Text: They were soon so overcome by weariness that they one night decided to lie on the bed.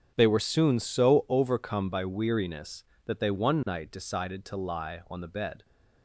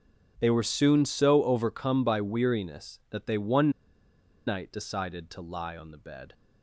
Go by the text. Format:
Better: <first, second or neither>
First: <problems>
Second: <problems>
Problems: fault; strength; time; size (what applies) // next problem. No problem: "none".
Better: first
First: starts louder than the rest; strong; until 1.1 s; 7.5 dB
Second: starts louder than the rest; until 1.3 s; 7 dB // pauses between "one" and "night"; noticeable; at 3.7 s; 0.76 s long